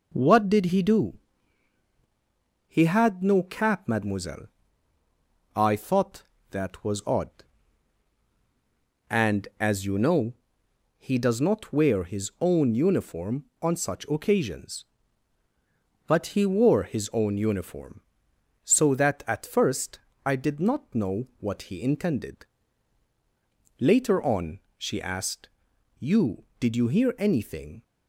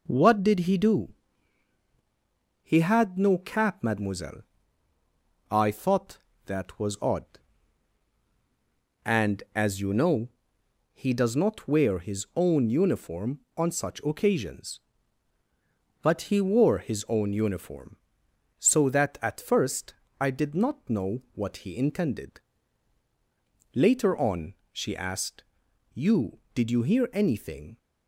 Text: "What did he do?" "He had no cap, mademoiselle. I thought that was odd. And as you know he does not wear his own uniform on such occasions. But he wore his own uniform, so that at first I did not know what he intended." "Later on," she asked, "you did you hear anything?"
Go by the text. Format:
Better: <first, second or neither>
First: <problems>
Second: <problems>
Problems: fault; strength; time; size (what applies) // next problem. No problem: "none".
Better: neither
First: pauses between "know" and "he"; noticeable; at 10.3 s; 0.64 s long // pauses between "first" and "I"; slight; at 19.9 s; 0.26 s long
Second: pauses between "know" and "he"; noticeable; at 10.2 s; 0.64 s long // pauses between "first" and "I"; slight; at 19.9 s; 0.26 s long